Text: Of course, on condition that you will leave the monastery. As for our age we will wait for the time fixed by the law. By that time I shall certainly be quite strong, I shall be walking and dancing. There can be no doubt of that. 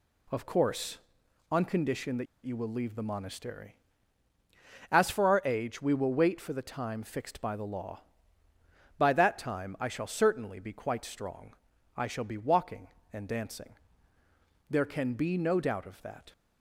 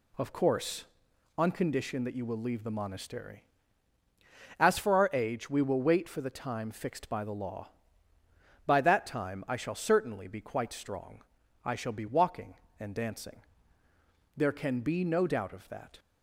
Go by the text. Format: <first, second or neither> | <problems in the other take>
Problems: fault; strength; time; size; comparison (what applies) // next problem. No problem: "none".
second | pauses between "that" and "you"; slight; at 2.2 s; 0.20 s long